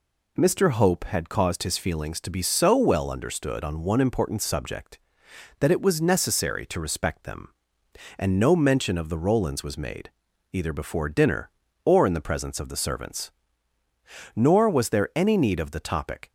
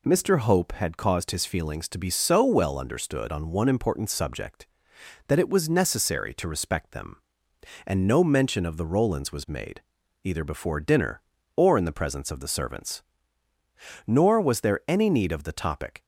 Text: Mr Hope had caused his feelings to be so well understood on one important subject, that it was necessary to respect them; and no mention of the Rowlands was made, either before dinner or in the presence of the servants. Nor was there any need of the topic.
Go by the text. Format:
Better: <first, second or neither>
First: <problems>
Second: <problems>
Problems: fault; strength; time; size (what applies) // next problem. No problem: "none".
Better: neither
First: none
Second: none